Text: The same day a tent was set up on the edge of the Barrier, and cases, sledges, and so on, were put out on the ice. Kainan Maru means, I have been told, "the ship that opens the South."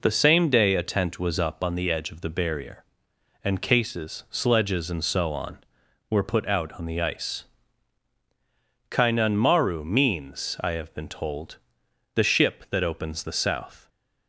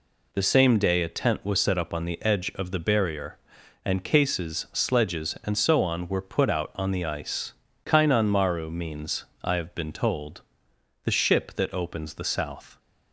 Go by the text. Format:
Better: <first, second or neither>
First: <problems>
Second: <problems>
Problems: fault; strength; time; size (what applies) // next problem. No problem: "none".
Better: second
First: skips "set"; at 1.3 s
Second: none